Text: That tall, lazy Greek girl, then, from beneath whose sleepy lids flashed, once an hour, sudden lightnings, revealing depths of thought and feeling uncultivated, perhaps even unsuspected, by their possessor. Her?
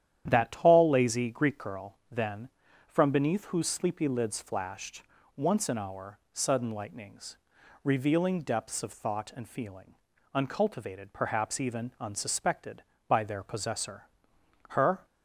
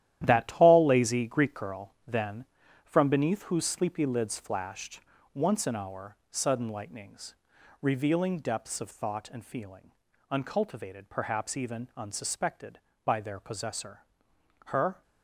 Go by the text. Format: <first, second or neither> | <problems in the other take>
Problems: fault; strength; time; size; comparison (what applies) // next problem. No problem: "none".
first | gets quieter; strong; throughout; 10 dB // starts louder than the rest; strong; until 1.2 s; 12 dB; strong in the first // pauses between "feeling" and "uncultivated"; at 9.9 s; 0.38 s long; also in the first